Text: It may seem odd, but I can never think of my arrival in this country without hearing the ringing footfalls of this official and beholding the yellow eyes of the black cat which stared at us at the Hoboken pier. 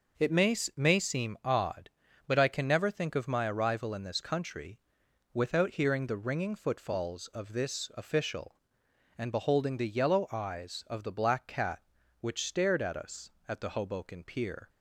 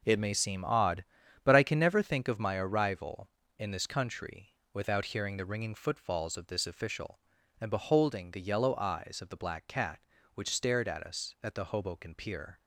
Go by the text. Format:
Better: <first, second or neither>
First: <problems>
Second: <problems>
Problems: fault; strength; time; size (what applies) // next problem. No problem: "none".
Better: second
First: says "may" twice; at 0.7 s // pauses between "country" and "without"; noticeable; at 4.7 s; 0.54 s long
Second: pauses between "country" and "without"; slight; at 4.4 s; 0.24 s long